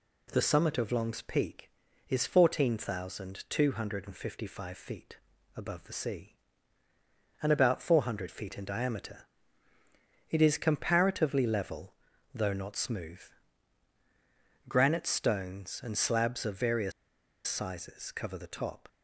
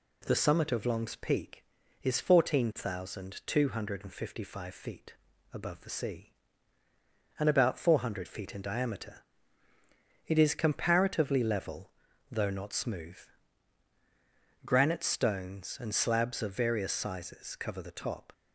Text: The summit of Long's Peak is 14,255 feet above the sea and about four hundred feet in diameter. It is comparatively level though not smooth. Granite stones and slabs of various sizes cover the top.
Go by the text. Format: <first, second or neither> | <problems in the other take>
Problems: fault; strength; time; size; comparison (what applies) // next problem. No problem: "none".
second | pauses between "feet" and "above"; at 5.1 s; 0.40 s long; also in the second // pauses between "level" and "though"; at 11.9 s; 0.42 s long; also in the second // pauses between "various" and "sizes"; noticeable; at 16.9 s; 0.55 s long